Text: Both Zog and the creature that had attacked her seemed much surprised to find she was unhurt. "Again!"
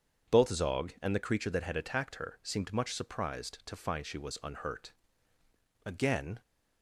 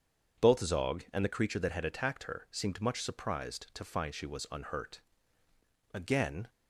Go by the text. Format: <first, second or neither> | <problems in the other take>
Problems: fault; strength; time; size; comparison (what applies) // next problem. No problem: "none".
neither | none